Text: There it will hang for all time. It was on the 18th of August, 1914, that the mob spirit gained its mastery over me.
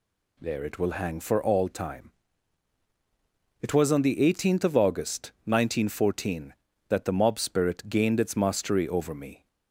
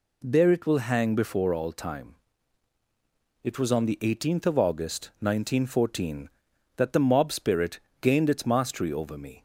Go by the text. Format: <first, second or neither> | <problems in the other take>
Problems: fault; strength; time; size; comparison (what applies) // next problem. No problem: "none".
first | says "before" for "for"; at 1.1 s // pauses between "spirit" and "gained"; slight; at 7.8 s; 0.20 s long